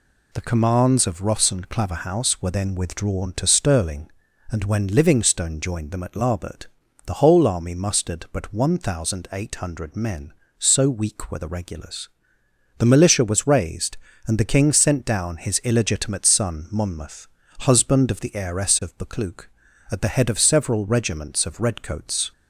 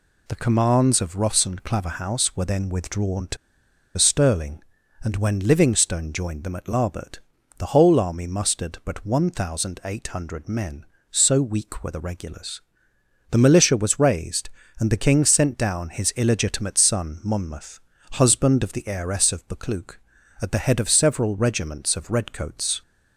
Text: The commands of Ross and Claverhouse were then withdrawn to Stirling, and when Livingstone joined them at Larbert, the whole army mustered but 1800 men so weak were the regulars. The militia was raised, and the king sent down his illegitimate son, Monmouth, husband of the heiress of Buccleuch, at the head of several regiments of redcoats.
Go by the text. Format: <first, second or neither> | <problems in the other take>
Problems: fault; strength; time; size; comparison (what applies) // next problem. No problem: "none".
first | pauses between "to" and "Stirling"; noticeable; at 3.3 s; 0.60 s long